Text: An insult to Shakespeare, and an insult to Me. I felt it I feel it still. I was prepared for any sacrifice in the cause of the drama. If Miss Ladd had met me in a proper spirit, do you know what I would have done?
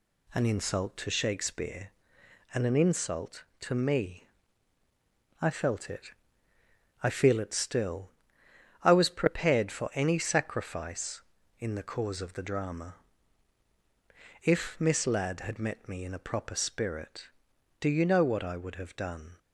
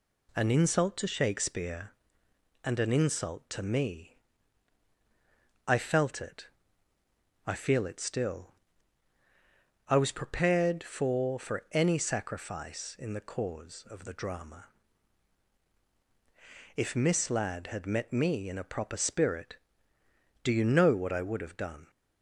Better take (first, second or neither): first